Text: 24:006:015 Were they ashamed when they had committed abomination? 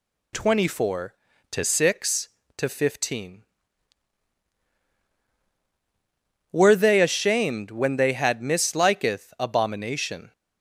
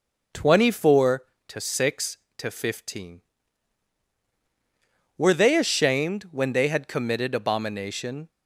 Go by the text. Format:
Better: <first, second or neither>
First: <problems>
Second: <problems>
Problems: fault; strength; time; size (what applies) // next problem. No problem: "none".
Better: second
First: says "misliketh" for "committed"; at 8.4 s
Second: none